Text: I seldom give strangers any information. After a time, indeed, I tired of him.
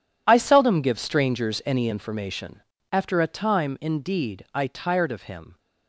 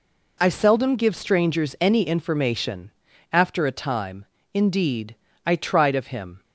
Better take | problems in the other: first | says "tried" for "tired"; at 5.5 s

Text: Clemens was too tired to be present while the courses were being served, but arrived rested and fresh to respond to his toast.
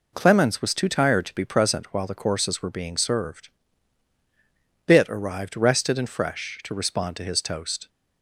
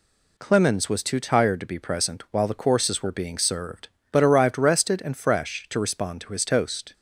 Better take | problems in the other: second | says "bit" for "but"; at 4.8 s

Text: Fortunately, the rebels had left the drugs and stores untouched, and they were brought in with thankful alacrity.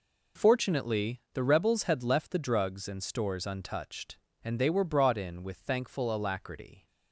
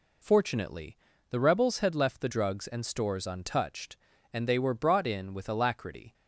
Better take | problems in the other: first | skips "thankful"; at 5.4 s

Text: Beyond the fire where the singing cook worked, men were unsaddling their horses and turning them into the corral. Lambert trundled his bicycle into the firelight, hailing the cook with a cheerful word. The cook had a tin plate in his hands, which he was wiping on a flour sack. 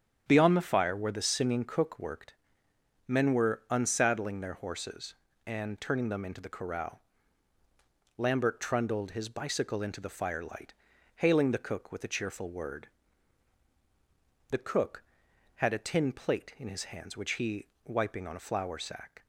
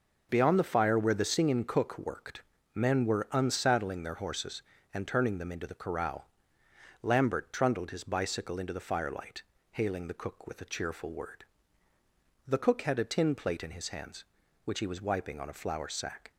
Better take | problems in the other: second | starts louder than the rest; strong; until 1.2 s; 8.5 dB // skips "was"; at 17.7 s

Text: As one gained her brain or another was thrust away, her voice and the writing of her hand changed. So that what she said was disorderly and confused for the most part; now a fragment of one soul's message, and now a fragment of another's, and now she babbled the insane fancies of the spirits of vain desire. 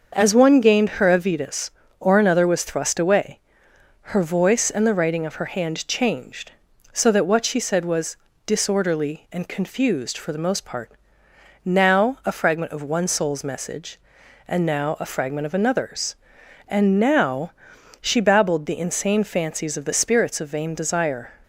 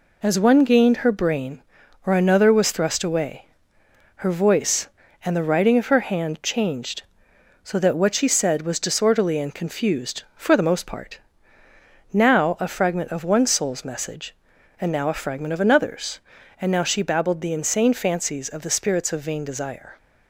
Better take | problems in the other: second | starts louder than the rest; until 1.1 s; 6.5 dB // says "avidus" for "brain"; at 1.0 s // pauses between "was" and "disorderly"; slight; at 8.1 s; 0.30 s long // pauses between "now" and "she"; noticeable; at 17.4 s; 0.50 s long

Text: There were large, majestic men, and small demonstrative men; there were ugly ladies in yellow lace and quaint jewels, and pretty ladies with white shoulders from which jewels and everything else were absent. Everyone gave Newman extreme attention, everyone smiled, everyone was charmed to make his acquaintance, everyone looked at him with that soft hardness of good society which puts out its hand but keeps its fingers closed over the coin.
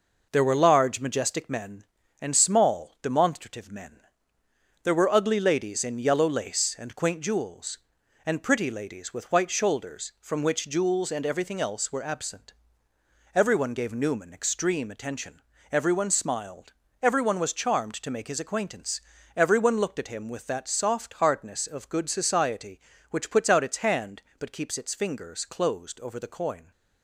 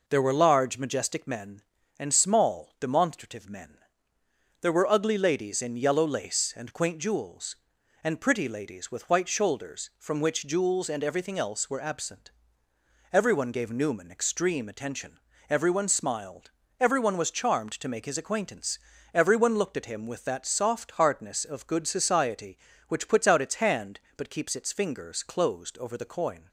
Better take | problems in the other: second | gets quieter; noticeable; throughout; 5 dB

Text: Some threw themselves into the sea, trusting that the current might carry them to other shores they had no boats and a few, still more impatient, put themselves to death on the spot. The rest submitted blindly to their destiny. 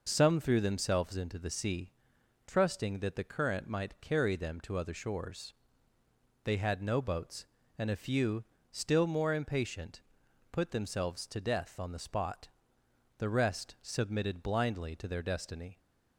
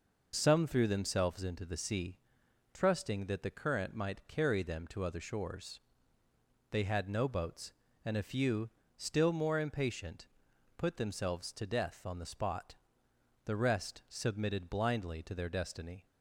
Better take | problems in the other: neither | pauses between "shores" and "they"; noticeable; the same in both

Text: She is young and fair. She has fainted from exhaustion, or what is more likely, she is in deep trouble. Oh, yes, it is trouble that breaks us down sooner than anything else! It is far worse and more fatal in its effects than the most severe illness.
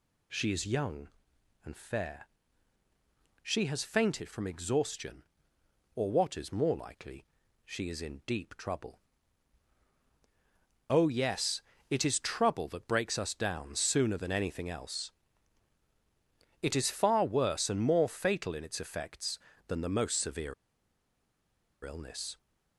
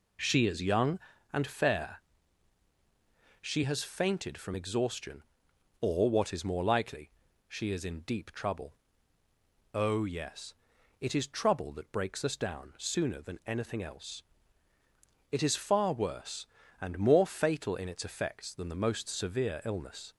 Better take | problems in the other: second | pauses between "severe" and "illness"; strong; at 20.5 s; 1.2 s long

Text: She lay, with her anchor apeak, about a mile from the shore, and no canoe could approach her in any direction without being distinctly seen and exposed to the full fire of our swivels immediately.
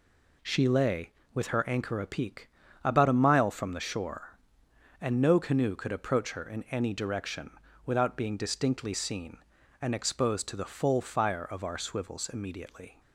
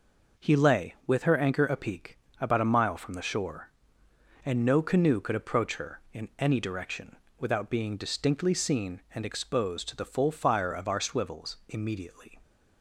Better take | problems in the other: first | says "He" for "She"; at 0.3 s // pauses between "direction" and "without"; slight; at 7.1 s; 0.22 s long; slight in the first

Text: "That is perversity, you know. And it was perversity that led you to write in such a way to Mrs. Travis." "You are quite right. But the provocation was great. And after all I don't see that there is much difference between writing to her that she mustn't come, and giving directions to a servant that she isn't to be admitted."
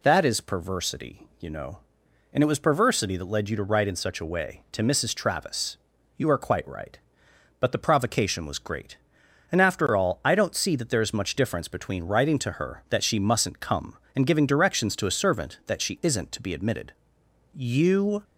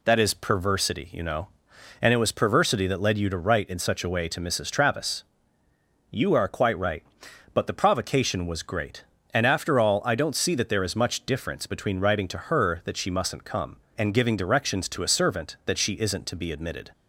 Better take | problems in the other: second | goes on to say "You"; noticeable; from 17.5 s on; 0.70 s long

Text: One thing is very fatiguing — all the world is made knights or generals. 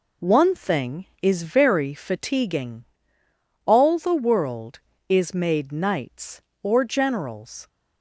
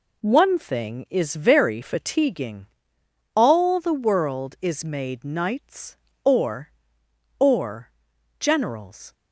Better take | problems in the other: first | says "or" twice; at 7.3 s

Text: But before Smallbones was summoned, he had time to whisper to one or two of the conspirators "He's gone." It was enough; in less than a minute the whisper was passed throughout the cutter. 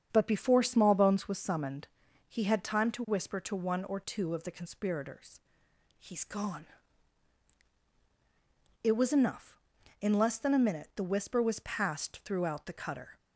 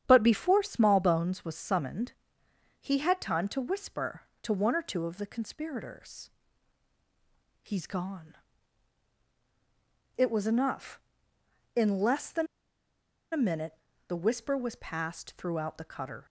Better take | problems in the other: first | starts louder than the rest; strong; until 1.0 s; 9 dB; strong in the first // pauses between "conspirators" and "He's"; strong; at 6.2 s; 1.3 s long; noticeable in the first // pauses between "than" and "a"; noticeable; at 12.4 s; 0.85 s long // pauses between "minute" and "the"; slight; at 13.7 s; 0.32 s long

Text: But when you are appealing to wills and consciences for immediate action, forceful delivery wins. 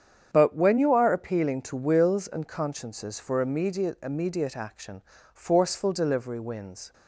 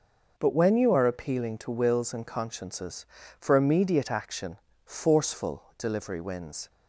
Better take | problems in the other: second | starts louder than the rest; strong; until 1.3 s; 8 dB // says "immediate" twice; at 4.0 s

